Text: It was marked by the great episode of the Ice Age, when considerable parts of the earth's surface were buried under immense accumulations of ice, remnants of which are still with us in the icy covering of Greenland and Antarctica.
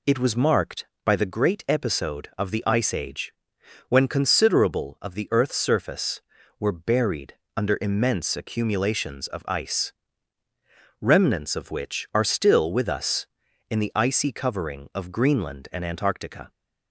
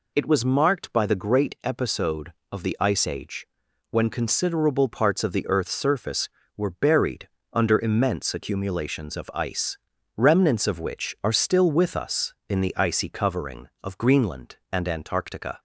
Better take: second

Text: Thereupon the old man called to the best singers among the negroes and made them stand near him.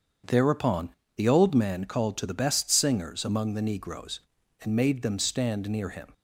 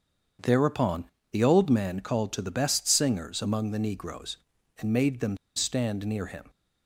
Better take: first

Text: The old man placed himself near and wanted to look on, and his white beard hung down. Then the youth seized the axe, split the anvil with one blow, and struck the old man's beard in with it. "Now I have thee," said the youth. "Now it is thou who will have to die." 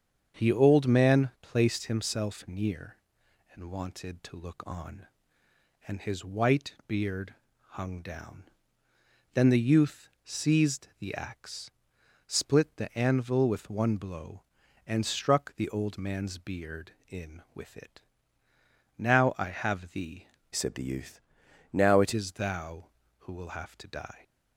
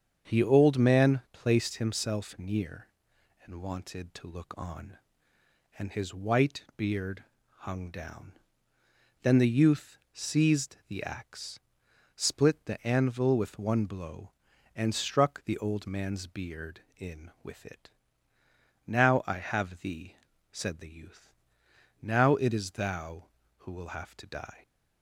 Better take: second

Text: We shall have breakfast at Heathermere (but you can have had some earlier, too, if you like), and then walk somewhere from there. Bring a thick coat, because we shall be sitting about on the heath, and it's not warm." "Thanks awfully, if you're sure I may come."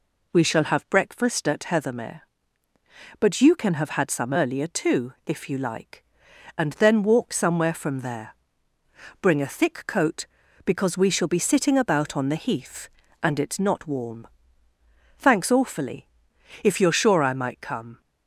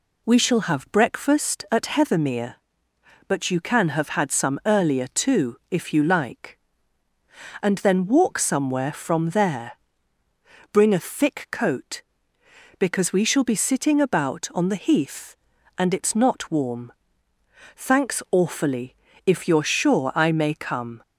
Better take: second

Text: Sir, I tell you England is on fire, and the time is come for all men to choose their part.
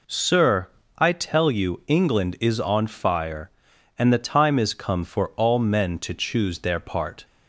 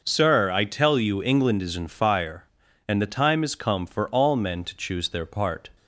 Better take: first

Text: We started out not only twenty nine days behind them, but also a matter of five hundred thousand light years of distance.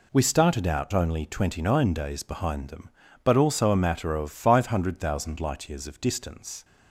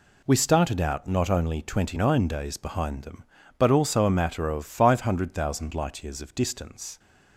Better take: second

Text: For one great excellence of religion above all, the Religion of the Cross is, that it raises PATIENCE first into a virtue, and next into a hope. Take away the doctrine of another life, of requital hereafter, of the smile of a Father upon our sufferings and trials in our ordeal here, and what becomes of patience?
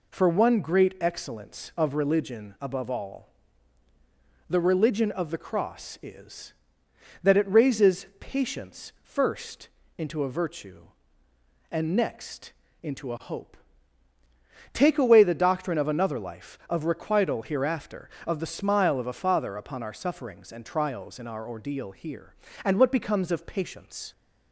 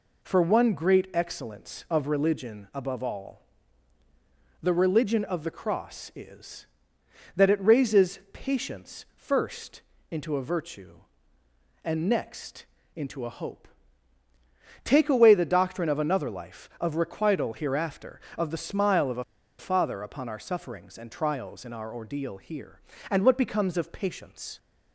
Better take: first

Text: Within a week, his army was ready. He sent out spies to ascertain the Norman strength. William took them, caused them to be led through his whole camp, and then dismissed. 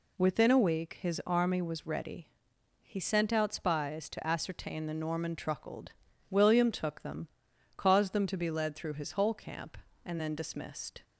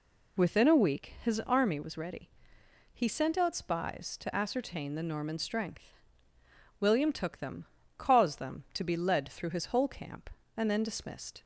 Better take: second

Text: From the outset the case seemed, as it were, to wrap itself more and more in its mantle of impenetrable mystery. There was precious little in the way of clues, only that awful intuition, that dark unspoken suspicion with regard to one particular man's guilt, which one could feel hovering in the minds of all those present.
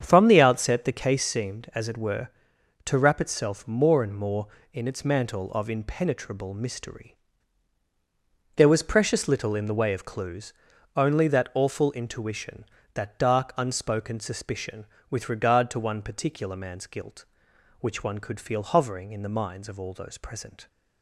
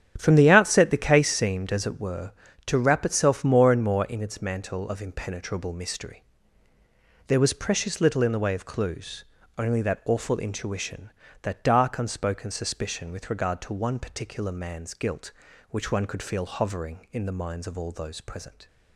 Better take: neither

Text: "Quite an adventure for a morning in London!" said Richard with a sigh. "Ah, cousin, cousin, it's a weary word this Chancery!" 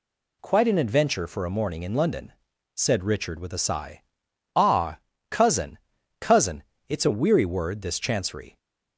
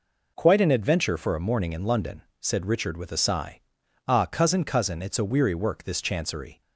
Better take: first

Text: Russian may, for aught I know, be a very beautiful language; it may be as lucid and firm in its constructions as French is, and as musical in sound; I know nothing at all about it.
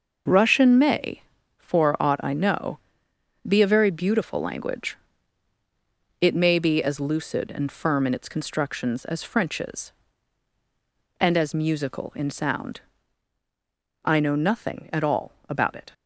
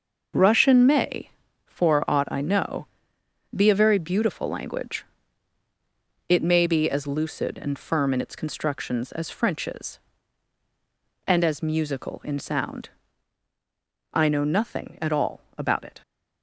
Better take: neither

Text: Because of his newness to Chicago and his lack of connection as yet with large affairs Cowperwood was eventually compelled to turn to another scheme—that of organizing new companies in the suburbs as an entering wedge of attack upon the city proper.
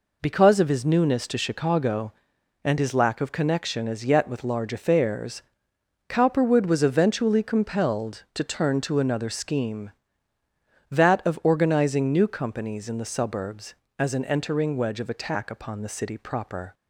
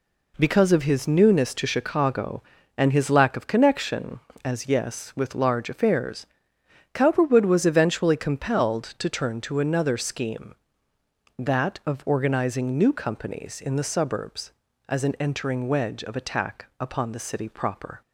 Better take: first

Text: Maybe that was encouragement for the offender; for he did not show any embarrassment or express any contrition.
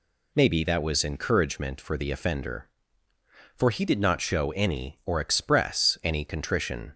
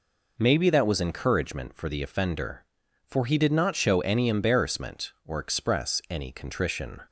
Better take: second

